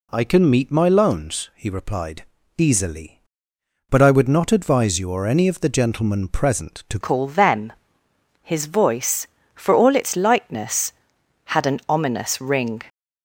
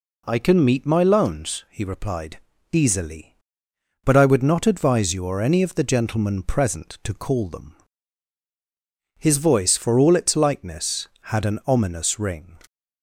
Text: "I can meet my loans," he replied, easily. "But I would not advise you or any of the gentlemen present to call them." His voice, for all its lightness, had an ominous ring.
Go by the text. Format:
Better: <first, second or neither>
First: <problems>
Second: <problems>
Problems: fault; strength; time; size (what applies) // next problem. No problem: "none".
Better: second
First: changes voice at "call"; from 7.0 s on; 5.8 s long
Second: none